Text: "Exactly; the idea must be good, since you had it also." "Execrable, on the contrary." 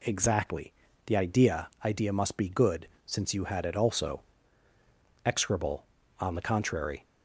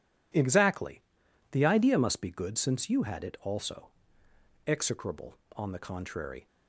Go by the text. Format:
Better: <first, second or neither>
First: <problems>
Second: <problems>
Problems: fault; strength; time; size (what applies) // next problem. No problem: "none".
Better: second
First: says "idea" twice; at 1.8 s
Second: none